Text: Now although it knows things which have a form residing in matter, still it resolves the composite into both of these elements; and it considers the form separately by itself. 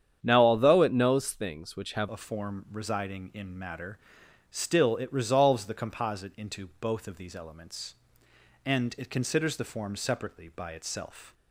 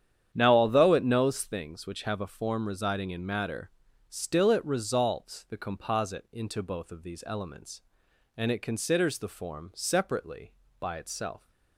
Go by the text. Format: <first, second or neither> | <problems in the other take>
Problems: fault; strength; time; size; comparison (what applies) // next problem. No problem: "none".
second | starts louder than the rest; strong; until 1.2 s; 9 dB; strong in the second // changes voice at "a"; from 2.0 s on; 9.3 s long